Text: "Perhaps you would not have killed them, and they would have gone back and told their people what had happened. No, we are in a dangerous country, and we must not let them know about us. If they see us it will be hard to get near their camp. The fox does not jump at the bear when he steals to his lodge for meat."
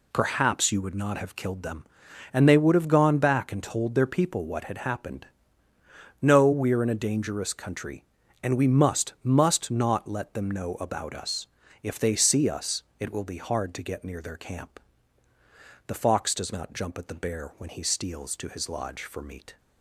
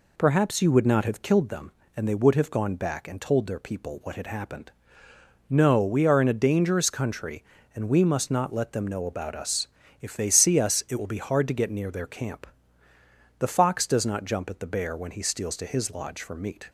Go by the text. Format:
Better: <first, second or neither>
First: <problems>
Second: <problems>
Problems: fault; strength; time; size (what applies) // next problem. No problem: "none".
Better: second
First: says "must" twice; at 9.2 s // pauses between "us" and "it"; slight; at 12.8 s; 0.18 s long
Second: none